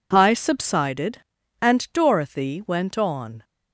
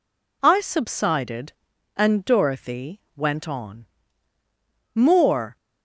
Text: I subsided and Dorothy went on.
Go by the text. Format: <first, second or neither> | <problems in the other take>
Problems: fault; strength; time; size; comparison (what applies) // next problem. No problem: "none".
first | pauses between "Dorothy" and "went"; slight; at 2.9 s; 0.16 s long // goes on to say "More"; noticeable; from 4.9 s on; 0.62 s long